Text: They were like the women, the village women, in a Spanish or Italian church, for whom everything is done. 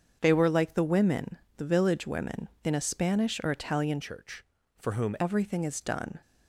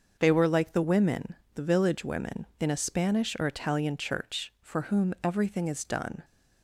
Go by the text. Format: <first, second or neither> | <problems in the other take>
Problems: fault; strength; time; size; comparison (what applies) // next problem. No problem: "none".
second | starts louder than the rest; strong; until 1.2 s; 7 dB; also in the second // changes voice from "church" to "whom"; from 4.0 to 5.1 s; 1.1 s long